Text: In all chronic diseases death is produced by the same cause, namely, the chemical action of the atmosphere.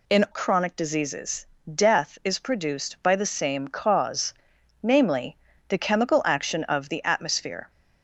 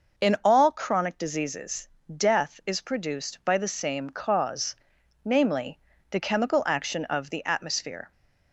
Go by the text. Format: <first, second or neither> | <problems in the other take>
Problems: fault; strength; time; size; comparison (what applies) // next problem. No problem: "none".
second | skips "all"; at 0.2 s // pauses between "diseases" and "death"; slight; at 1.4 s; 0.28 s long; slight in the second